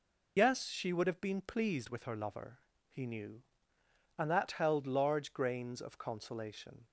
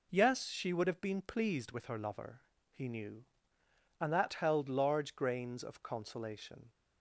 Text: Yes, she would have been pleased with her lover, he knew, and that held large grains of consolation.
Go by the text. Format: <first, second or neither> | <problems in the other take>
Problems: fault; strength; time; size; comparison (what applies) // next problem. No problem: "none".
second | loses the start of "Yes"; at 0.3 s; 55 ms